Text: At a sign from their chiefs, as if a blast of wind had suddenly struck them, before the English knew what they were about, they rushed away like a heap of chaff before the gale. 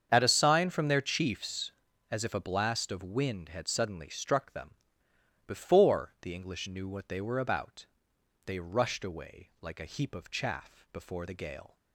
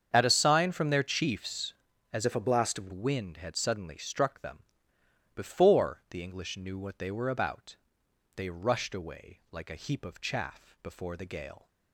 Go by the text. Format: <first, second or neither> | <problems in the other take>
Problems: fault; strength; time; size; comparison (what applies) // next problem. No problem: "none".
first | starts louder than the rest; strong; until 1.1 s; 7.5 dB; strong in the first // changes voice from "if" to "of"; from 2.2 to 2.8 s; 0.6 s long